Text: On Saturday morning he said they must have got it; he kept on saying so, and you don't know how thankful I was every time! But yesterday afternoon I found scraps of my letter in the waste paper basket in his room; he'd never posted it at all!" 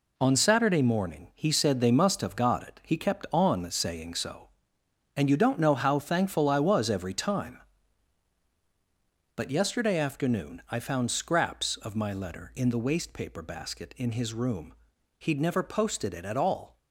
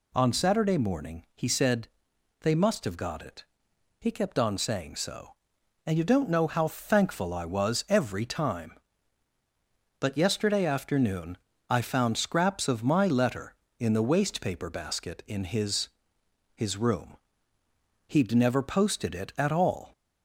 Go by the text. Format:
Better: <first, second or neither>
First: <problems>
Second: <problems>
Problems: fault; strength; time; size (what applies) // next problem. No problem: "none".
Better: first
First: none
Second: pauses between "said" and "they"; noticeable; at 1.8 s; 0.54 s long // pauses between "afternoon" and "I"; slight; at 11.3 s; 0.32 s long // says "his" twice; at 16.5 s